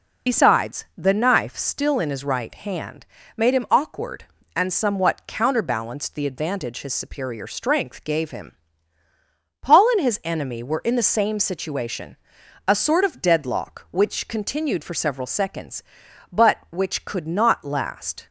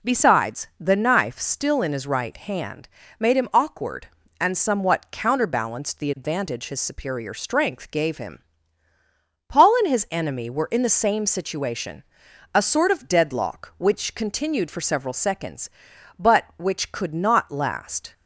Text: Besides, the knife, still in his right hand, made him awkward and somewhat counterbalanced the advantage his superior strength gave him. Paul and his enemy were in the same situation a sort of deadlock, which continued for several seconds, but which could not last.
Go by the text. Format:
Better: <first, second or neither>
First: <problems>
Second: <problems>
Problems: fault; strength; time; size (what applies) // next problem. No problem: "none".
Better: second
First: loses the start of "Besides"; at 0.2 s; 65 ms // pauses between "situation" and "a"; noticeable; at 12.1 s; 0.52 s long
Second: pauses between "situation" and "a"; noticeable; at 12.0 s; 0.52 s long